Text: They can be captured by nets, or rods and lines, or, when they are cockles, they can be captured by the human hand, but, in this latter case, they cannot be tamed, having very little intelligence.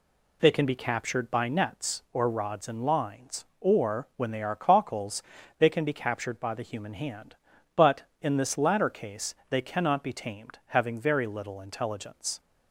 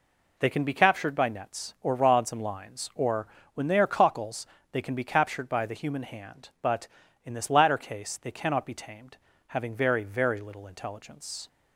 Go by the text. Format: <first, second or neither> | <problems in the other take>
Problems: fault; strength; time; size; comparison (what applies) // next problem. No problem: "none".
first | says "very" twice; at 10.0 s